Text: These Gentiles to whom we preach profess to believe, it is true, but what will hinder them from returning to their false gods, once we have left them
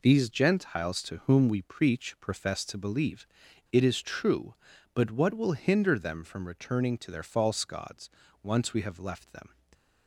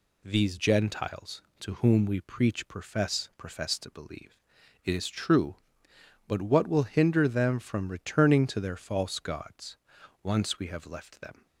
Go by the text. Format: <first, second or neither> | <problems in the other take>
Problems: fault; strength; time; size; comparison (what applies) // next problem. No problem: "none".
first | says "profess" twice; at 3.3 s